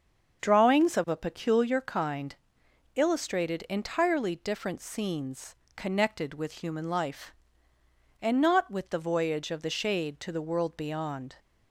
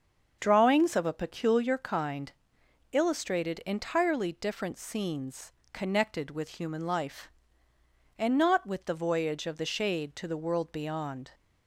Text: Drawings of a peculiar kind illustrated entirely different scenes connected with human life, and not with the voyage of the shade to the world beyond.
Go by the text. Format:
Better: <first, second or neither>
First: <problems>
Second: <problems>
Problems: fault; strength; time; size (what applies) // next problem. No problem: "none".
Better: neither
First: starts louder than the rest; until 1.4 s; 7 dB // pauses between "kind" and "illustrated"; noticeable; at 2.3 s; 0.62 s long // pauses between "scenes" and "connected"; slight; at 5.5 s; 0.22 s long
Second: starts louder than the rest; until 1.4 s; 6.5 dB // pauses between "kind" and "illustrated"; noticeable; at 2.3 s; 0.62 s long // pauses between "scenes" and "connected"; slight; at 5.5 s; 0.22 s long